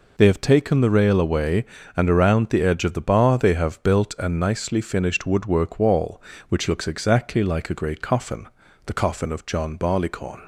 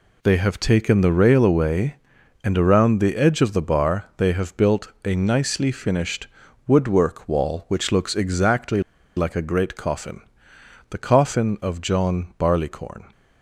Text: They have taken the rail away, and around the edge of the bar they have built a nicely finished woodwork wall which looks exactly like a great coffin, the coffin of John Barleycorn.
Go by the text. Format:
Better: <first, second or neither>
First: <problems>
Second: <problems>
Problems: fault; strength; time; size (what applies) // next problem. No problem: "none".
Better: first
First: none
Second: pauses between "finished" and "woodwork"; at 6.2 s; 0.40 s long // pauses between "exactly" and "like"; slight; at 8.8 s; 0.34 s long